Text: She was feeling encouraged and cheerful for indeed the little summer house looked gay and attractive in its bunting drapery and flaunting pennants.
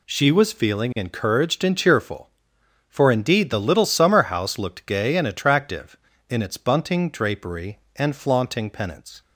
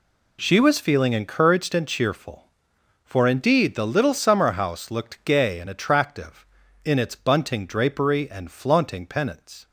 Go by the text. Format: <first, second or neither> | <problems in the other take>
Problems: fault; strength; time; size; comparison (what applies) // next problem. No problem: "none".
neither | none